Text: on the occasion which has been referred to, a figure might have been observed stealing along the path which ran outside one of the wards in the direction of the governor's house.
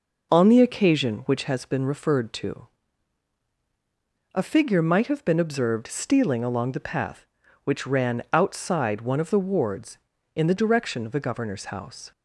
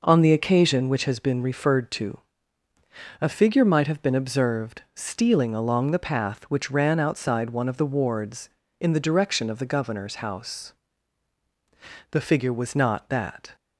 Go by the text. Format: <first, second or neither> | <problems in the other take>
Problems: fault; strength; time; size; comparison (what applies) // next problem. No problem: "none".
first | goes on to say "The figure was not that"; from 12.1 s on; 1.4 s long